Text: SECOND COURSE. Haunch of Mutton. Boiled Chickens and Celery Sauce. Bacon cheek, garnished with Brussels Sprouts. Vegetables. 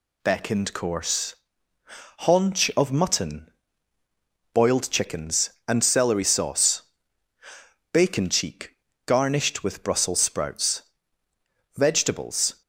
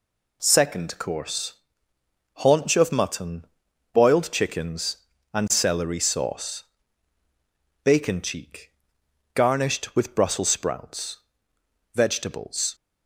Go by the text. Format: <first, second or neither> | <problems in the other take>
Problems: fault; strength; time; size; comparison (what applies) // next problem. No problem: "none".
second | says "Beckoned" for "SECOND"; at 0.2 s